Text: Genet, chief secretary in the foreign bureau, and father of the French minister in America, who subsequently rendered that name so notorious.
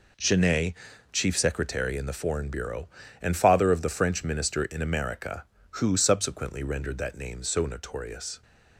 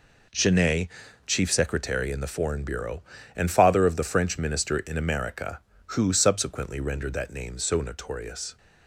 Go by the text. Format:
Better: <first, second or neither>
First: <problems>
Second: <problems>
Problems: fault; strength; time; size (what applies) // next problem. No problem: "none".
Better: neither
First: none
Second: none